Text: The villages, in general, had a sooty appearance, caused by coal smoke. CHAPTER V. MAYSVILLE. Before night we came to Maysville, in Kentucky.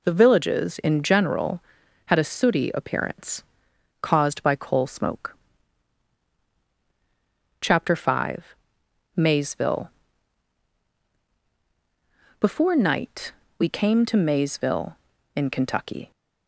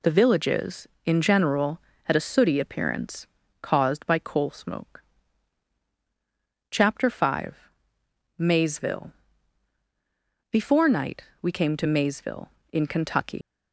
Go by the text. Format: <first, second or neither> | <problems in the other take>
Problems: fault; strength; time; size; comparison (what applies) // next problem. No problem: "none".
first | pauses between "night" and "we"; slight; at 11.2 s; 0.18 s long; slight in the first // leaves "Kentucky" unfinished; at 13.4 s; 80 ms